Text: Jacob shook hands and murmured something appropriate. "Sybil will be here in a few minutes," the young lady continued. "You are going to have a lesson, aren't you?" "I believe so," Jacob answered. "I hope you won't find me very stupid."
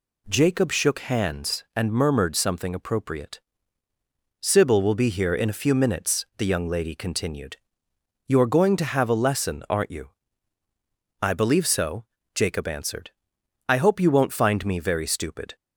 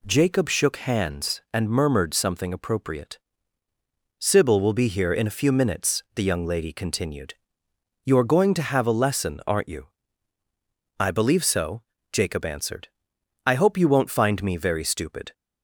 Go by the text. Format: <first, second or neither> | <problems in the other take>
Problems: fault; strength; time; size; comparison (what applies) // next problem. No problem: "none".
neither | none